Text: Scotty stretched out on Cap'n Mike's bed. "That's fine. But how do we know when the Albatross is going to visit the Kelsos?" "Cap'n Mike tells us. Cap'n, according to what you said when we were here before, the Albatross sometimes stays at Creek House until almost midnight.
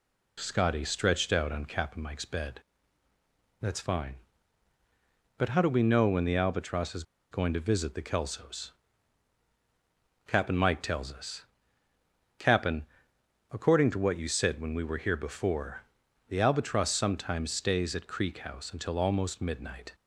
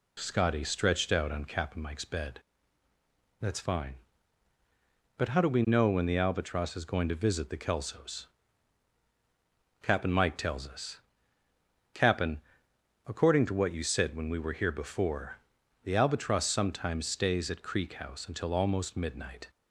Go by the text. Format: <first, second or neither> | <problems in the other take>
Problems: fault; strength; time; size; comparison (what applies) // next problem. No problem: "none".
second | pauses between "is" and "going"; slight; at 7.0 s; 0.28 s long